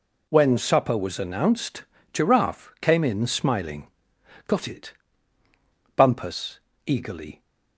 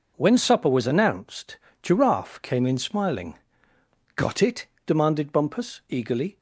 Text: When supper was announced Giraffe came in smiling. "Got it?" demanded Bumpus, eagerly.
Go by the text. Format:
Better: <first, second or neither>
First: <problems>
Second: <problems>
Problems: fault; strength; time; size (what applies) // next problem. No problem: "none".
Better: second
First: pauses between "announced" and "Giraffe"; slight; at 1.8 s; 0.28 s long // skips "demanded"; at 5.4 s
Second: pauses between "announced" and "Giraffe"; slight; at 1.5 s; 0.24 s long